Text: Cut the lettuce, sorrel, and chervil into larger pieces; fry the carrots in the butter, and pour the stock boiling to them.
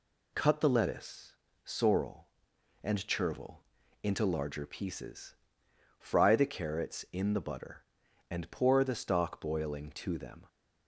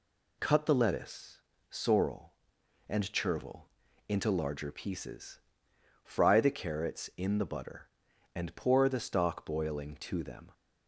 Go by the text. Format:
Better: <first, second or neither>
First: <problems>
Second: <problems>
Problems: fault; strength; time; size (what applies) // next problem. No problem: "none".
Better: neither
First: pauses between "chervil" and "into"; at 3.6 s; 0.40 s long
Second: pauses between "chervil" and "into"; at 3.6 s; 0.40 s long